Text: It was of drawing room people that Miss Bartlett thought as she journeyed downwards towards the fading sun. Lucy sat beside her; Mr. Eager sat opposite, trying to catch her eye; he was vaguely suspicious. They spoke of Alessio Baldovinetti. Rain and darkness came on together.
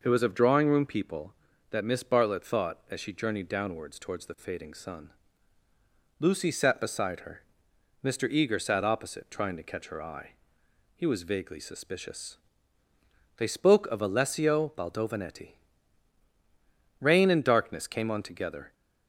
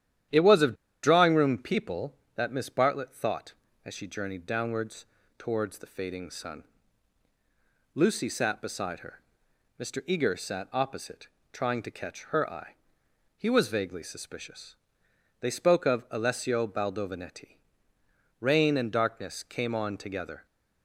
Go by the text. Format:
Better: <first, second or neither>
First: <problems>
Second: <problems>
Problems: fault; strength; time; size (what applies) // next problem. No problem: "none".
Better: first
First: none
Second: starts louder than the rest; strong; until 1.5 s; 11 dB // pauses between "of" and "drawing"; slight; at 0.7 s; 0.28 s long // pauses between "downwards" and "towards"; slight; at 5.0 s; 0.34 s long